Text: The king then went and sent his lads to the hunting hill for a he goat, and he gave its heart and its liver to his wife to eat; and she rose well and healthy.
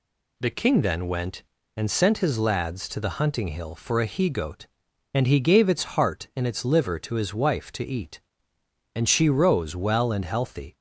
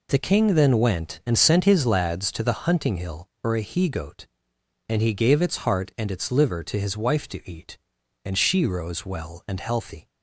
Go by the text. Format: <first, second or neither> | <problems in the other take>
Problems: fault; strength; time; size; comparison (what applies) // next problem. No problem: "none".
neither | none